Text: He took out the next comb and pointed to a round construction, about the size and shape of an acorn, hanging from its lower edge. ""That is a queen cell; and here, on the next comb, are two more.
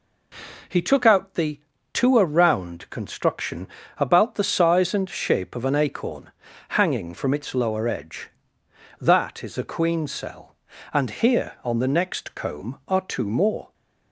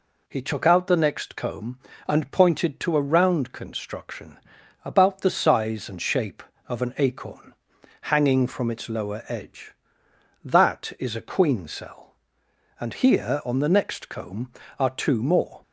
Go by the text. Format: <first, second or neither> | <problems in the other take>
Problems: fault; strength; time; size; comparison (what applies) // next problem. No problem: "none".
second | skips "next comb and pointed"; at 1.7 s